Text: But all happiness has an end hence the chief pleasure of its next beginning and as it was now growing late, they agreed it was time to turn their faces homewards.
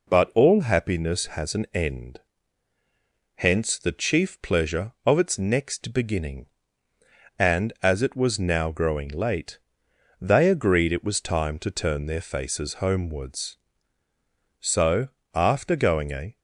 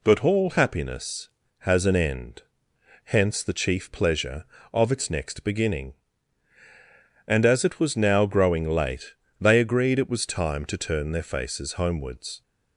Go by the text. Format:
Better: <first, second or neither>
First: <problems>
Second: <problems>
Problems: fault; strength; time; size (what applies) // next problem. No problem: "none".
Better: second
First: pauses between "end" and "hence"; at 2.2 s; 1.1 s long // goes on to say "So after going a"; strong; from 14.6 s on; 1.7 s long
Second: pauses between "end" and "hence"; noticeable; at 2.4 s; 0.64 s long